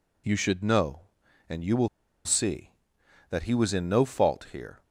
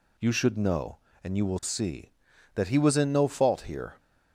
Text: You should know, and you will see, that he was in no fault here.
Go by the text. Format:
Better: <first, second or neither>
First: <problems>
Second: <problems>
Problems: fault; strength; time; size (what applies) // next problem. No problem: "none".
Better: second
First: pauses between "will" and "see"; at 1.8 s; 0.38 s long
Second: none